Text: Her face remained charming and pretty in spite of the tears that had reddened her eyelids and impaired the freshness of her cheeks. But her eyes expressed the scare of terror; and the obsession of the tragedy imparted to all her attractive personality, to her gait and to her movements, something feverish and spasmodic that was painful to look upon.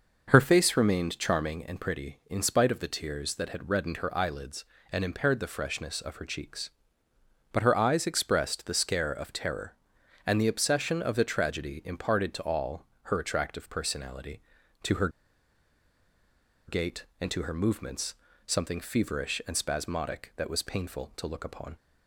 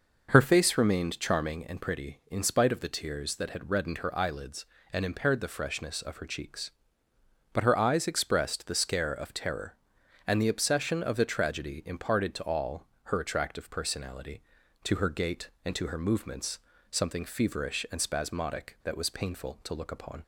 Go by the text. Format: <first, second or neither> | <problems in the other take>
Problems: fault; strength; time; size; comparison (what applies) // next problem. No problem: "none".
second | pauses between "all" and "her"; slight; at 12.8 s; 0.20 s long; slight in the second // pauses between "her" and "gait"; strong; at 15.0 s; 1.5 s long